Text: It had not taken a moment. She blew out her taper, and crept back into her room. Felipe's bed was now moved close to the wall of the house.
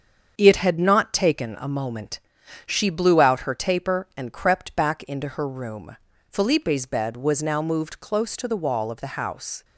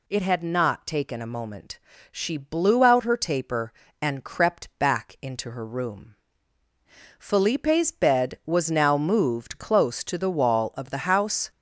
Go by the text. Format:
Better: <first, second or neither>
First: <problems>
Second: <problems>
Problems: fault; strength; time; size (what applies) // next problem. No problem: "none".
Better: second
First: gets quieter; noticeable; throughout; 6 dB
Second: none